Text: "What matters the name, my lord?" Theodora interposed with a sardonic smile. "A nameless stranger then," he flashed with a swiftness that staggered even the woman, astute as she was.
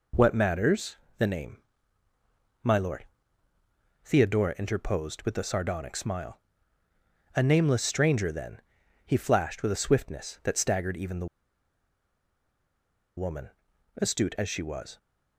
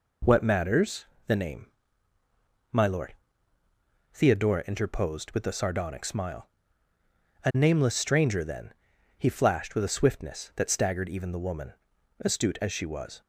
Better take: second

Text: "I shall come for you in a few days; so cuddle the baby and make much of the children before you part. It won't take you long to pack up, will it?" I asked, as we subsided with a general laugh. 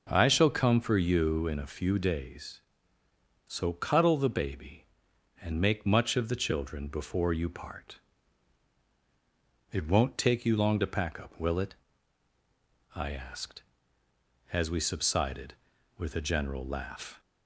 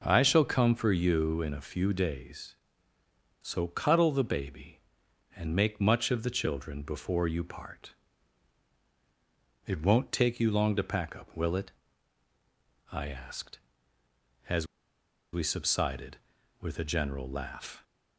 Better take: first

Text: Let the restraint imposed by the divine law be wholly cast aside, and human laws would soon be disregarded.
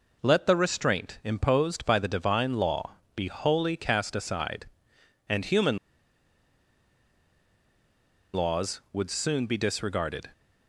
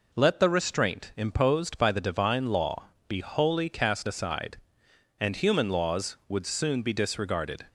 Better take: second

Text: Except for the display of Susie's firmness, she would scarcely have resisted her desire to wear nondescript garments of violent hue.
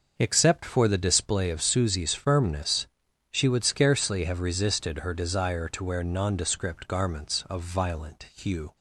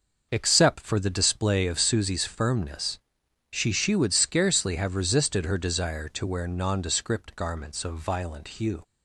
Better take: first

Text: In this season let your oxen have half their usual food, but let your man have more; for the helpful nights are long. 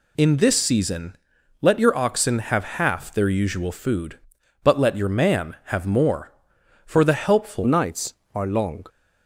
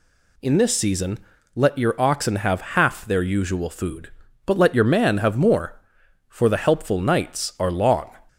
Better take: second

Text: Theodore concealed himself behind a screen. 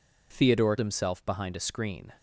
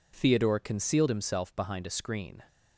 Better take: second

